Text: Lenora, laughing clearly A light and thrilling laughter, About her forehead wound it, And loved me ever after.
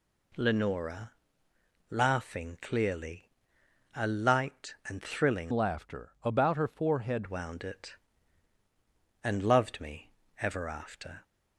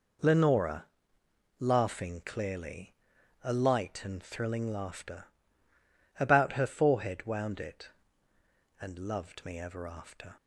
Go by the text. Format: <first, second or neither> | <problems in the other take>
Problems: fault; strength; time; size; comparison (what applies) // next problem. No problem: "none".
second | pauses between "clearly" and "A"; noticeable; at 3.2 s; 0.66 s long; noticeable in the second // changes voice from "laughter" to "forehead"; from 5.5 to 7.2 s; 1.7 s long // pauses between "me" and "ever"; slight; at 10.1 s; 0.28 s long